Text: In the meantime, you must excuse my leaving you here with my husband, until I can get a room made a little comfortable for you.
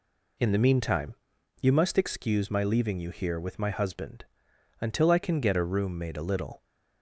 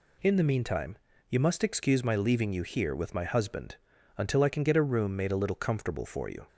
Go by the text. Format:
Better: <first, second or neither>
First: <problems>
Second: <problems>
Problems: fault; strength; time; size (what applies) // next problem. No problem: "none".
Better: second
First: stops before "comfortable for you"; at 6.6 s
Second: none